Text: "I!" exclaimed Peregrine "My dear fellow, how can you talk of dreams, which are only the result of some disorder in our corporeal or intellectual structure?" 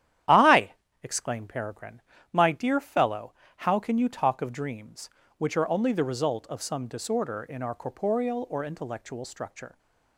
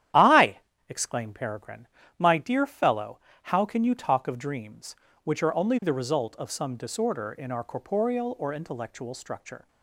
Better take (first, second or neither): neither